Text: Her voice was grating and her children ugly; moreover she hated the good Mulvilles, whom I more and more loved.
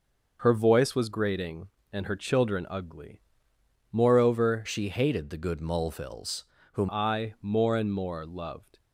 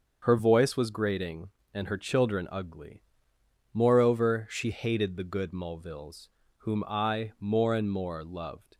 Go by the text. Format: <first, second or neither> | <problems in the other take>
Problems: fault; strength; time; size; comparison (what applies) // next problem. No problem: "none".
second | starts louder than the rest; noticeable; until 1.4 s; 6 dB; also in the second // changes voice from "she" to "whom"; from 4.6 to 6.8 s; 2.2 s long